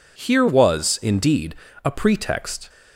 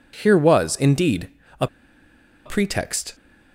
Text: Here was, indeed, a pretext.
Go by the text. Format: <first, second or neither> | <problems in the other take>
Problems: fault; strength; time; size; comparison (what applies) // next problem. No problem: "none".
first | pauses between "a" and "pretext"; noticeable; at 1.6 s; 0.79 s long